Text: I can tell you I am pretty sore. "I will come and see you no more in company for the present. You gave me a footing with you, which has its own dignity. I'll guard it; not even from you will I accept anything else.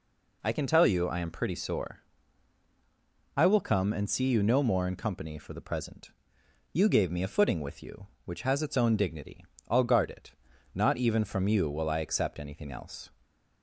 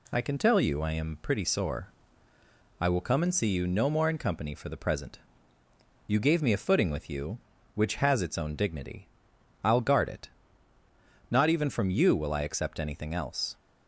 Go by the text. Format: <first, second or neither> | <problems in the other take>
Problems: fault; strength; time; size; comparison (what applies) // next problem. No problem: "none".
neither | none